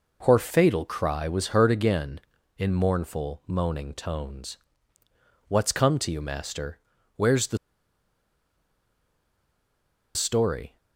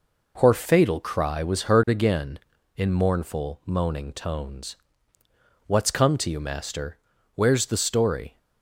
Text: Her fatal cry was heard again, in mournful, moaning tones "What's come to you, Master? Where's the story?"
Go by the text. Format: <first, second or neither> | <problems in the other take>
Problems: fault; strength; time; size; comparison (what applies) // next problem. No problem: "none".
second | pauses between "tones" and "What's"; noticeable; at 4.5 s; 0.90 s long; noticeable in the second // pauses between "the" and "story"; strong; at 7.5 s; 2.5 s long